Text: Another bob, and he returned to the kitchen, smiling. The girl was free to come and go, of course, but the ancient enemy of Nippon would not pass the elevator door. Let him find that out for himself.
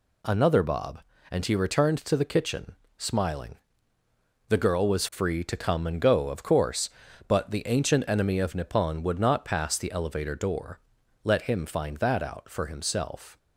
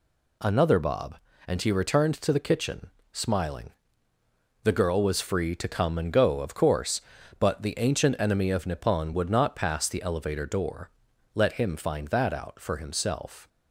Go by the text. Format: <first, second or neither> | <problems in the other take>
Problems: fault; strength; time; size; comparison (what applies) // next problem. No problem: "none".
neither | none